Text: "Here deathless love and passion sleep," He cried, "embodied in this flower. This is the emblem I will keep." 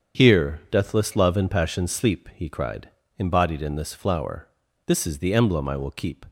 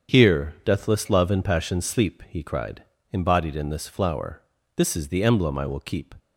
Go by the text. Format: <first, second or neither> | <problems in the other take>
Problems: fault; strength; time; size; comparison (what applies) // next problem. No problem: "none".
neither | starts louder than the rest; strong; the same in both